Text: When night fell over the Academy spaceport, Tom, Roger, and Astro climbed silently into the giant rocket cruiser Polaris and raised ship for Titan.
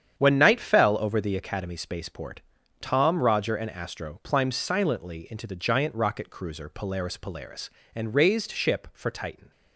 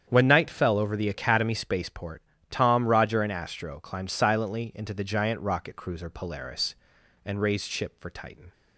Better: second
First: starts louder than the rest; strong; until 1.2 s; 8.5 dB // says "Polaris" twice; at 7.1 s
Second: starts louder than the rest; strong; until 1.1 s; 8.5 dB

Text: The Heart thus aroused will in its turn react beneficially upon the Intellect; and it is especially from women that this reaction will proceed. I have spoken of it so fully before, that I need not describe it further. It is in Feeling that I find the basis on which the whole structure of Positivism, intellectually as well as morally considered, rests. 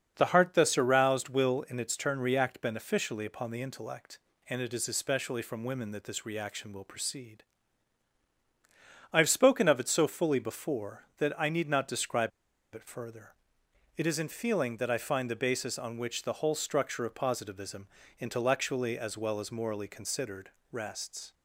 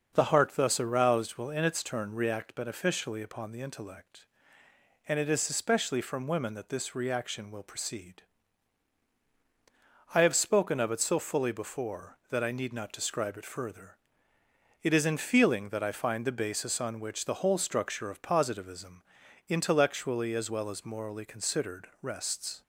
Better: second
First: starts louder than the rest; until 1.1 s; 6.5 dB // pauses between "describe" and "it"; at 12.3 s; 0.44 s long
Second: starts louder than the rest; until 1.1 s; 6.5 dB

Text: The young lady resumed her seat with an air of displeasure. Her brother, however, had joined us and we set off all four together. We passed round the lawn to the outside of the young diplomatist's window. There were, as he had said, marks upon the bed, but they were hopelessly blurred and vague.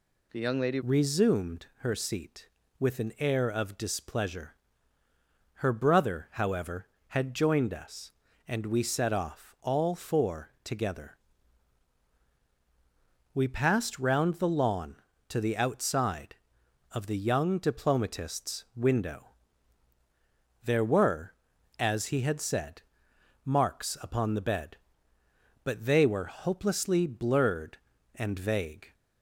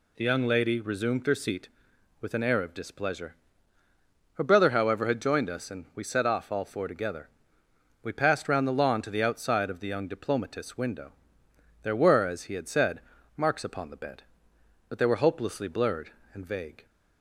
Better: second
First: changes voice at "resumed"; from 0.8 s on; 28.1 s long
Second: none

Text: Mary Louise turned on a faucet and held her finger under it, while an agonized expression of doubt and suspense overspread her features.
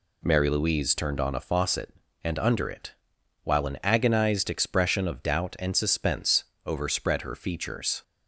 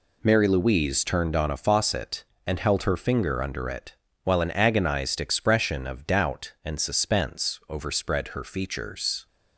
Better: second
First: skips "held her finger"; at 2.3 s // pauses between "suspense" and "overspread"; slight; at 6.4 s; 0.20 s long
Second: none

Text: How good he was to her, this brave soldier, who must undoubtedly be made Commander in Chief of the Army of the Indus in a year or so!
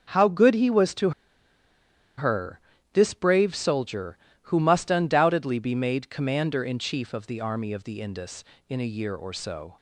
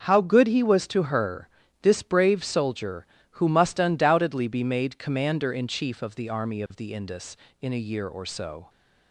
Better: second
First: starts louder than the rest; until 2.2 s; 7 dB // pauses between "to" and "her"; at 1.1 s; 1.0 s long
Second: starts louder than the rest; until 1.0 s; 7 dB

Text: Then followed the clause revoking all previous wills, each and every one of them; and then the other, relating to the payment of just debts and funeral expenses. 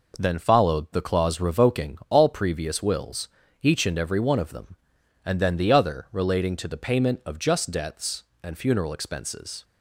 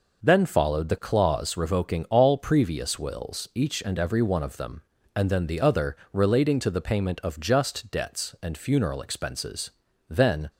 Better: first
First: none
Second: goes on to say "Then"; slight; from 10.0 s on; 0.40 s long

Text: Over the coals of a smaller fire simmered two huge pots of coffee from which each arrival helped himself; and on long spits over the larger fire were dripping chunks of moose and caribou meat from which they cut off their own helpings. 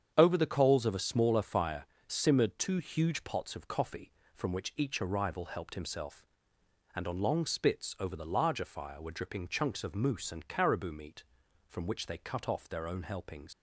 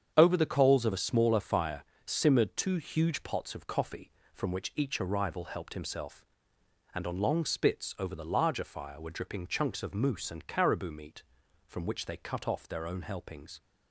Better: second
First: starts louder than the rest; strong; until 1.1 s; 8 dB // pauses between "fire" and "simmered"; slight; at 1.8 s; 0.20 s long // leaves "helpings" unfinished; at 13.5 s; 90 ms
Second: starts louder than the rest; strong; until 1.1 s; 8 dB // pauses between "fire" and "simmered"; slight; at 1.8 s; 0.20 s long

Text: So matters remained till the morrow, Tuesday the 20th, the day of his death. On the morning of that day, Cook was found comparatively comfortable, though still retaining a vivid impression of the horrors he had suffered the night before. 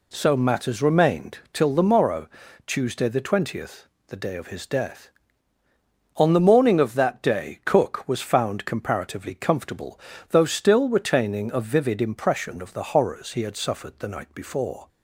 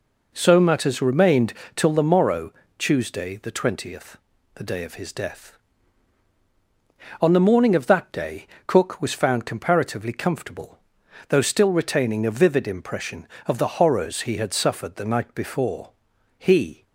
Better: first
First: pauses between "remained" and "till"; slight; at 1.3 s; 0.16 s long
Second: pauses between "remained" and "till"; slight; at 1.5 s; 0.22 s long // goes on to say "He"; slight; from 16.3 s on; 0.46 s long

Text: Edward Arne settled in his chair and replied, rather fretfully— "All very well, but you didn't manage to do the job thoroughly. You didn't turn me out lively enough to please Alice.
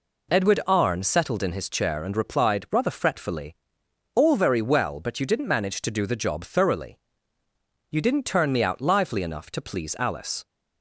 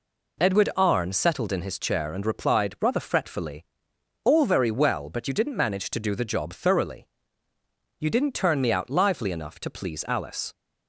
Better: neither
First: none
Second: none

